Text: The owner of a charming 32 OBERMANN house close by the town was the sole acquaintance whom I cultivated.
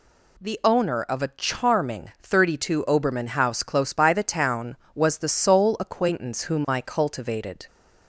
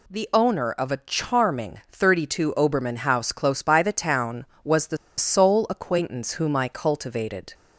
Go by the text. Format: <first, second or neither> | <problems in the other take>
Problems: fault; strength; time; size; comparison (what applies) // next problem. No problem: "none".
first | pauses between "the" and "sole"; slight; at 4.9 s; 0.21 s long